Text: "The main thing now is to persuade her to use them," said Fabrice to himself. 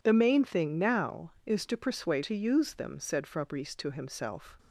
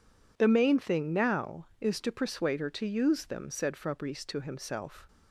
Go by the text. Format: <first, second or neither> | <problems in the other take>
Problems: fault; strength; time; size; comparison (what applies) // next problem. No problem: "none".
second | skips "her"; at 2.2 s